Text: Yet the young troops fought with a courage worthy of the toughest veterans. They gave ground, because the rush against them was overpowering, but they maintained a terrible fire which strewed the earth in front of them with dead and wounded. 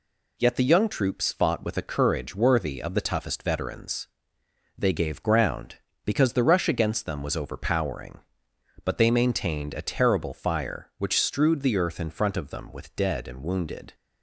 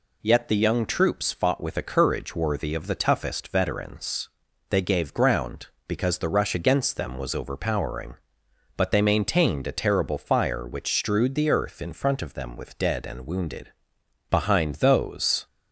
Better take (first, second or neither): first